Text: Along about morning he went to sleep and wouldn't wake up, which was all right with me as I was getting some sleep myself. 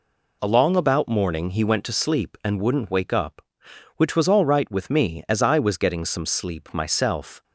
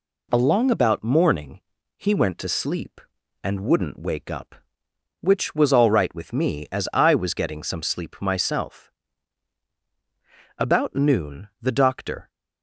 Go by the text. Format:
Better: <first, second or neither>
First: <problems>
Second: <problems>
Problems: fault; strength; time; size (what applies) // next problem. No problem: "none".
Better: first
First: none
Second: pauses between "morning" and "he"; slight; at 1.5 s; 0.36 s long // goes on to say "About noon the doctor"; strong; from 10.5 s on; 1.7 s long